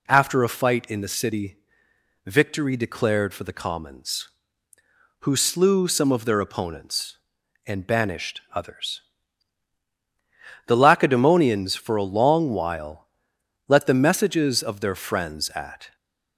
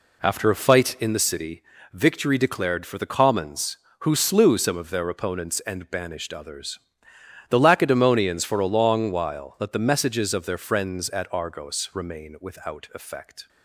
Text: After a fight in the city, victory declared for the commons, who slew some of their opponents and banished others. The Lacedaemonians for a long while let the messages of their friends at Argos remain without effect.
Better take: second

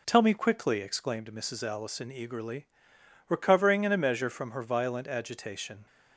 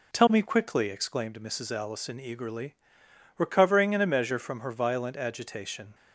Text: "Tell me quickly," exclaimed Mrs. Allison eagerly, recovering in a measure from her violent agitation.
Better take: neither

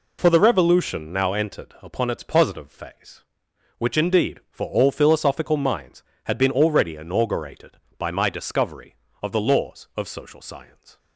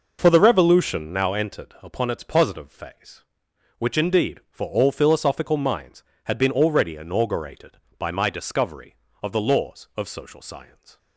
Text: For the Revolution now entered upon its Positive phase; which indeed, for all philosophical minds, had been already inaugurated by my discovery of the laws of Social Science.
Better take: first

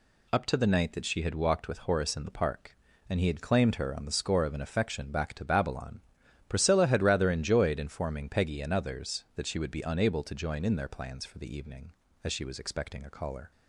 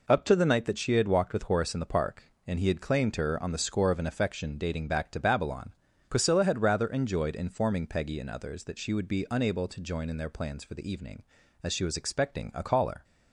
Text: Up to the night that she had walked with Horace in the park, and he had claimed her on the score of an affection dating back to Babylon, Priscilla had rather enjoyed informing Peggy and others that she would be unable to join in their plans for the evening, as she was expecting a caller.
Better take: second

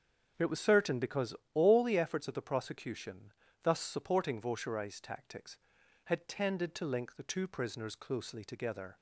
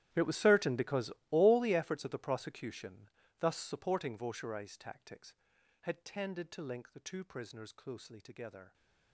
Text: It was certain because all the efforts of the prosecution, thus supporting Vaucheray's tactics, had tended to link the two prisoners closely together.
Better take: first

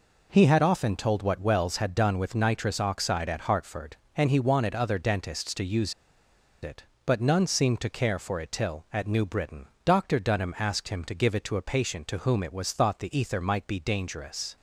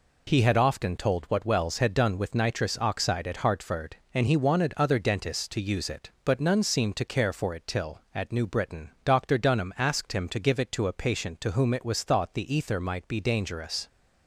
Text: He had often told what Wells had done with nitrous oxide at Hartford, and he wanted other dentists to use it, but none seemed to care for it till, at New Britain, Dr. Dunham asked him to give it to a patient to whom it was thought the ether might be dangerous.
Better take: second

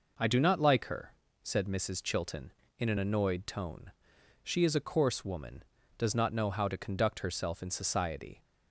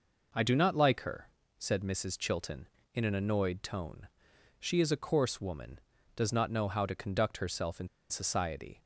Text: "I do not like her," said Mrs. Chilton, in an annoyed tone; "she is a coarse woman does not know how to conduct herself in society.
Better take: first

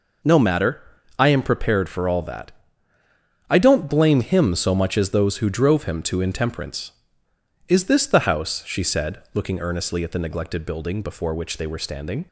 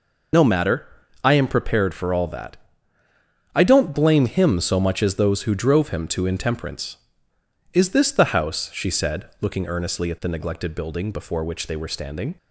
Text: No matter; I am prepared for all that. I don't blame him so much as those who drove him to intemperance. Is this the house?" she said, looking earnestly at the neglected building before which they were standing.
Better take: first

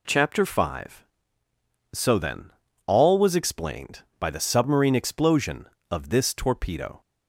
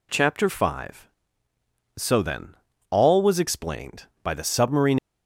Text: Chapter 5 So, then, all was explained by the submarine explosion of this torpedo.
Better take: first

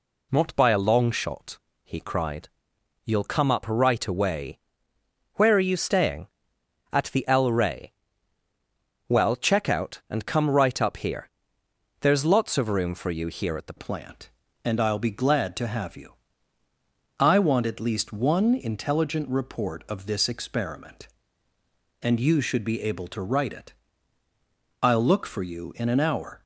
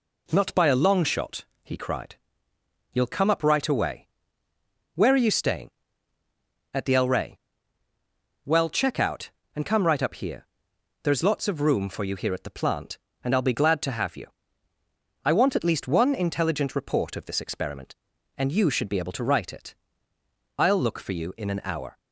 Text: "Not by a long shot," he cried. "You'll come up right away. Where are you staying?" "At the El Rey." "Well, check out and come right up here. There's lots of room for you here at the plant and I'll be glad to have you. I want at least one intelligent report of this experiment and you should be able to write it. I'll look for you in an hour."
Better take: second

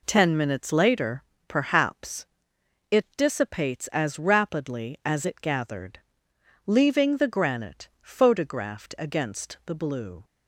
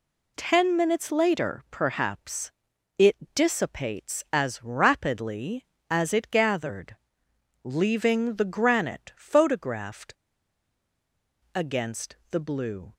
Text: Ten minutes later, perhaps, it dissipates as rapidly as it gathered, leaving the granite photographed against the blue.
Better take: first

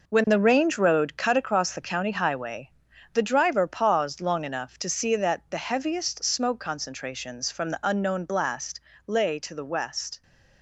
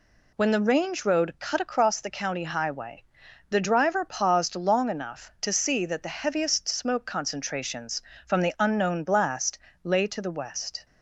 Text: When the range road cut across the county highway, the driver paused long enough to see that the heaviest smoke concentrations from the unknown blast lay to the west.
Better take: second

